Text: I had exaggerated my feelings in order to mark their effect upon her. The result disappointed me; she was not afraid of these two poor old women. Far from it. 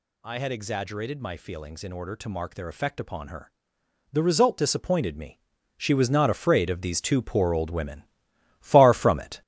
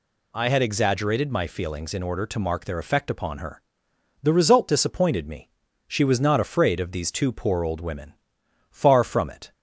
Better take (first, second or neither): second